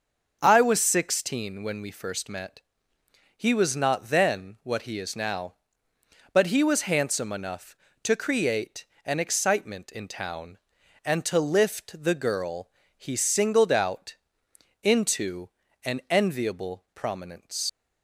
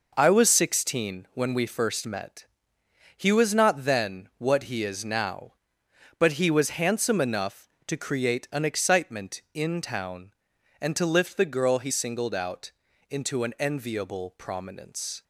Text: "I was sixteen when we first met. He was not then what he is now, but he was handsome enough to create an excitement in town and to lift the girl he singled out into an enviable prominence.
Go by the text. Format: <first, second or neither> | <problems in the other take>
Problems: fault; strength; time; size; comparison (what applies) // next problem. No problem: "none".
second | starts louder than the rest; until 1.4 s; 6.5 dB // pauses between "create" and "an"; slight; at 8.8 s; 0.20 s long // pauses between "girl" and "he"; slight; at 12.6 s; 0.28 s long // pauses between "out" and "into"; noticeable; at 14.1 s; 0.66 s long; slight in the second // pauses between "into" and "an"; slight; at 15.4 s; 0.34 s long // leaves "prominence" unfinished; at 17.6 s; 60 ms